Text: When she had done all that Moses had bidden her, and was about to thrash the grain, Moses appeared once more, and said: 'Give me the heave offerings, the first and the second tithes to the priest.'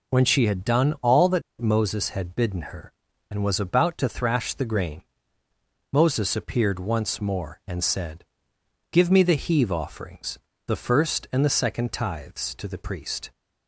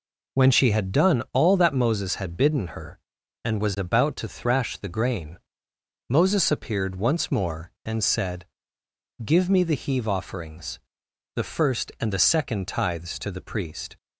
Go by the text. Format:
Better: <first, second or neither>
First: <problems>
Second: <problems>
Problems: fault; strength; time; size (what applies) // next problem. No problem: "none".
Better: second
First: pauses between "that" and "Moses"; slight; at 1.4 s; 0.19 s long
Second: none